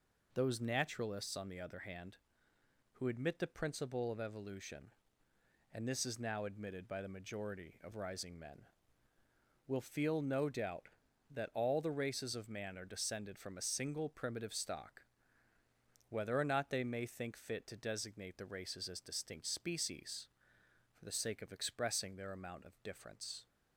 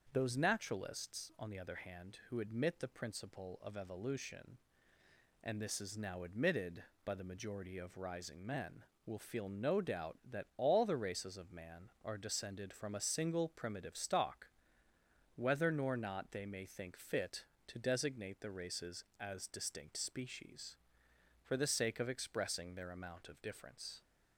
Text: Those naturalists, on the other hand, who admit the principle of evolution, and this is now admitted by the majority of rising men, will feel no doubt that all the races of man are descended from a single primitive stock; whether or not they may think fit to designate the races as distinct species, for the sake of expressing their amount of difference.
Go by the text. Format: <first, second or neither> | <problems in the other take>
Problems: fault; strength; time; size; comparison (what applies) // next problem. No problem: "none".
first | starts louder than the rest; until 1.1 s; 6.5 dB // says "nor" for "or"; at 15.6 s